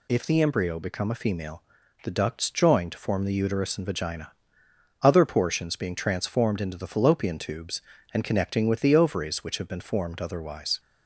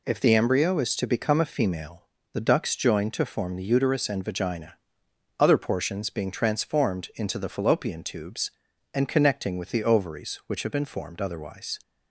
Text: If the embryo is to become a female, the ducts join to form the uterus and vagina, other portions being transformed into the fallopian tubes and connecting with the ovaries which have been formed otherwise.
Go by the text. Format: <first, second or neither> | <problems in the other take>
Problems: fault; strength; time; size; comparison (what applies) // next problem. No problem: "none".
second | skips "is to"; at 0.7 s